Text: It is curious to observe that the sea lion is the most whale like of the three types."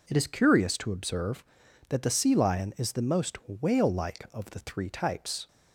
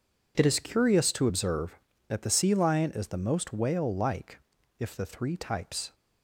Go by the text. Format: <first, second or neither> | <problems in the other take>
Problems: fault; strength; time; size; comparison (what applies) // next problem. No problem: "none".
first | says "if" for "of"; at 4.8 s